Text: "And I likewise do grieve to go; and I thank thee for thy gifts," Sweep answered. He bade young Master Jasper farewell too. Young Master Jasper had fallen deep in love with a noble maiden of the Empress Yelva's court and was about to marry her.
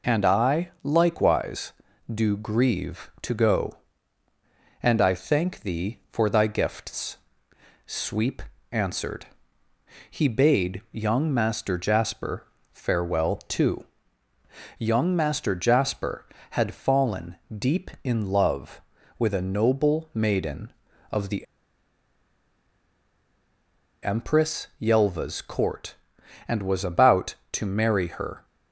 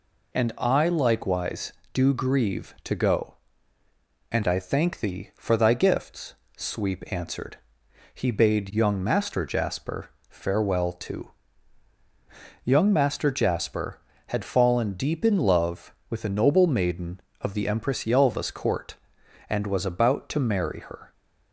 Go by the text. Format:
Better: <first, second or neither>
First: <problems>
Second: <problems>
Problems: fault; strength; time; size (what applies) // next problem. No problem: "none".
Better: second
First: pauses between "Sweep" and "answered"; slight; at 8.4 s; 0.28 s long // pauses between "Jasper" and "farewell"; slight; at 12.4 s; 0.26 s long // pauses between "fallen" and "deep"; slight; at 17.3 s; 0.20 s long // pauses between "the" and "Empress"; strong; at 21.4 s; 2.5 s long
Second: pauses between "Jasper" and "farewell"; slight; at 10.0 s; 0.22 s long